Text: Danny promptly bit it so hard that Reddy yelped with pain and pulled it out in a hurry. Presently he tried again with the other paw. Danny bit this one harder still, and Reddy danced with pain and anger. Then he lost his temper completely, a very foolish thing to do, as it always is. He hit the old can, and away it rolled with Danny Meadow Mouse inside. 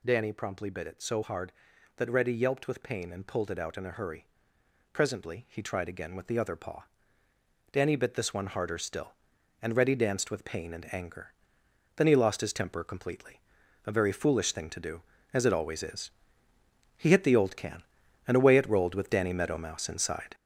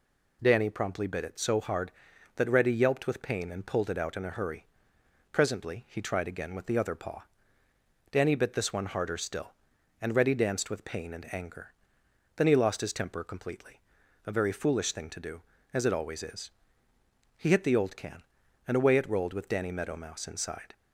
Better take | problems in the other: second | gets louder; noticeable; throughout; 5.5 dB

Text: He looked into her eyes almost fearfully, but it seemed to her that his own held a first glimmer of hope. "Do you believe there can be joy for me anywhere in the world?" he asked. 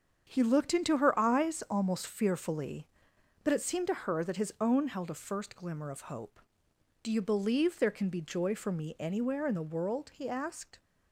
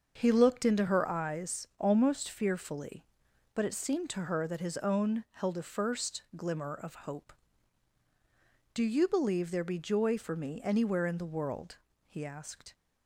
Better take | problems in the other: first | starts louder than the rest; until 1.2 s; 6.5 dB; strong in the first // skips "can"; at 9.6 s

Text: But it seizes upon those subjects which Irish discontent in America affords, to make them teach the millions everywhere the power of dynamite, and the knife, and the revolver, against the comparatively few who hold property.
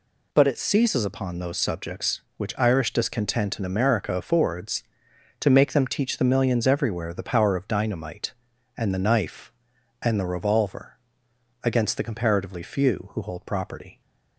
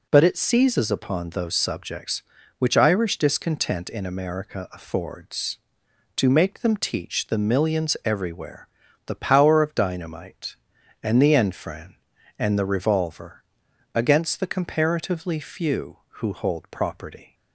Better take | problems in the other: first | pauses between "everywhere" and "the"; at 8.6 s; 0.38 s long // says "enfran" for "knife"; at 11.3 s

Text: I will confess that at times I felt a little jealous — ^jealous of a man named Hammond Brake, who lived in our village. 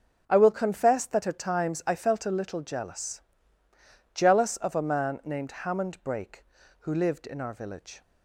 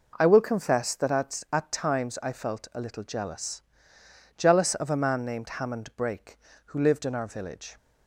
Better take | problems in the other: first | says "at" twice; at 1.5 s

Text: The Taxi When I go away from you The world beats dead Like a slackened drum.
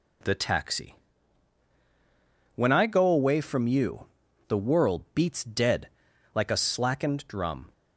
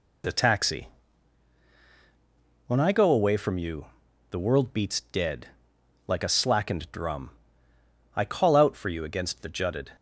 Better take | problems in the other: first | pauses between "Taxi" and "When"; strong; at 0.8 s; 1.7 s long; strong in the first // pauses between "you" and "The"; noticeable; at 3.8 s; 0.46 s long; also in the first // pauses between "dead" and "Like"; noticeable; at 5.4 s; 0.58 s long; noticeable in the first // goes on to say "I call out for you against the jutted"; strong; from 8.1 s on; 1.7 s long

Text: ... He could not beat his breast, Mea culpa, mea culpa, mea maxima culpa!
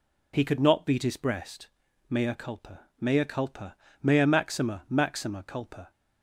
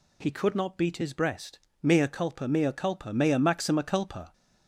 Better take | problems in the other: second | says "maxima" twice; at 4.8 s

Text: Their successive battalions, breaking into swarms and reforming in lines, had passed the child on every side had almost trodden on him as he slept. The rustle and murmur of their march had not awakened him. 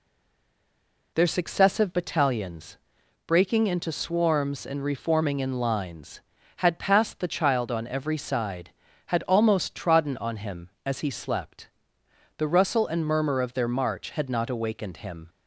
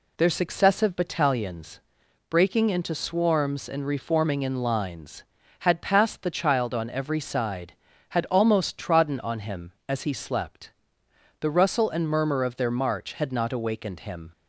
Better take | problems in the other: second | stays silent before the first word; until 1.1 s; 1.1 s long

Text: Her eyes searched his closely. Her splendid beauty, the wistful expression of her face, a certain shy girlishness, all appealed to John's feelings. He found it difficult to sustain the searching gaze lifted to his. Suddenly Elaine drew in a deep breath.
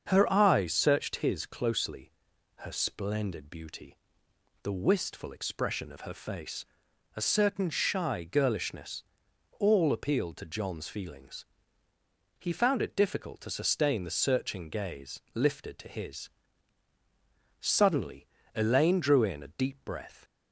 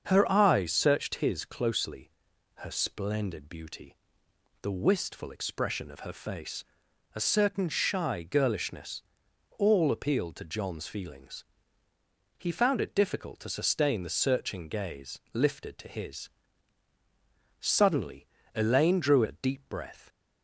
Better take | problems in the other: first | starts louder than the rest; until 1.1 s; 7 dB; also in the first // pauses between "gaze" and "lifted"; slight; at 15.1 s; 0.16 s long; slight in the first // pauses between "Suddenly" and "Elaine"; slight; at 18.2 s; 0.26 s long; slight in the first // skips "in"; at 19.2 s

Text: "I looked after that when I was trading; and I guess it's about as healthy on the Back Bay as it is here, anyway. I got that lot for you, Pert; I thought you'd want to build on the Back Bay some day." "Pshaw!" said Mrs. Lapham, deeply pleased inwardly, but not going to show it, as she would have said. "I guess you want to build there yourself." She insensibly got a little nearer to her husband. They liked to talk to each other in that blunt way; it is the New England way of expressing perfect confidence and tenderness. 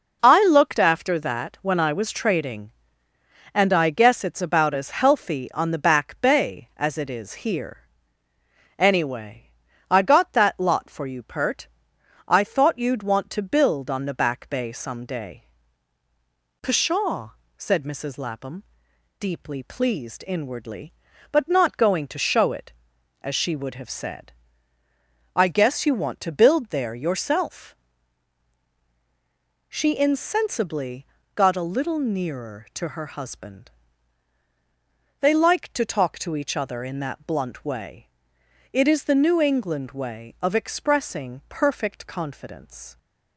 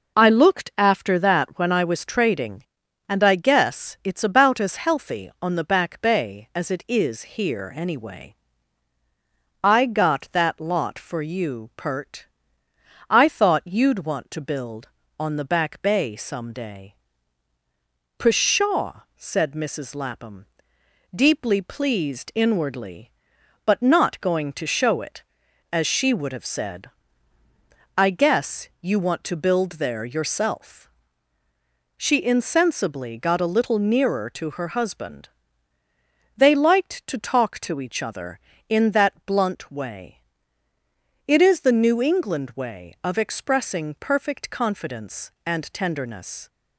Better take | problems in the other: second | pauses between "insensibly" and "got"; slight; at 31.0 s; 0.30 s long // stops before "and tenderness"; at 42.9 s

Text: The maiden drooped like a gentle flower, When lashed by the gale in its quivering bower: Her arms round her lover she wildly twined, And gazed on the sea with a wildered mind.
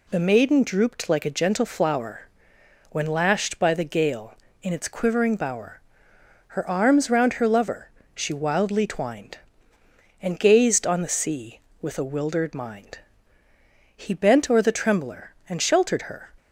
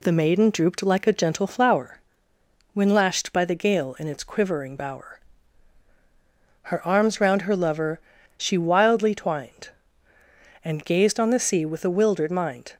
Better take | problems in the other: second | pauses between "lover" and "she"; slight; at 7.8 s; 0.26 s long; slight in the second // goes on to say "He bent o'er the trembler and sheltered her"; strong; from 13.9 s on; 2.3 s long

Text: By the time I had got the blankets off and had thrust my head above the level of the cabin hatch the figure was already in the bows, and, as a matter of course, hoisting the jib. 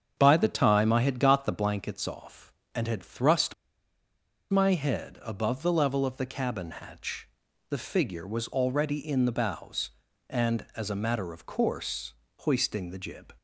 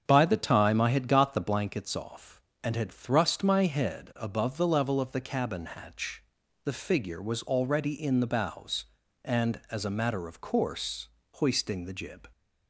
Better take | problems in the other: second | starts louder than the rest; strong; until 1.1 s; 7.5 dB; strong in the second // pauses between "thrust" and "my"; noticeable; at 3.5 s; 0.96 s long // pauses between "hatch" and "the"; at 7.2 s; 0.40 s long; also in the second

